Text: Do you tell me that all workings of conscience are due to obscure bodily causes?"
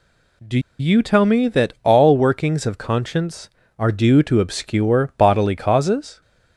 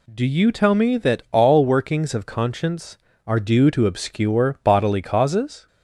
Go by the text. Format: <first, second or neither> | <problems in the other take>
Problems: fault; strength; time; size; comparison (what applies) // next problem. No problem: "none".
second | pauses between "Do" and "you"; slight; at 0.5 s; 0.20 s long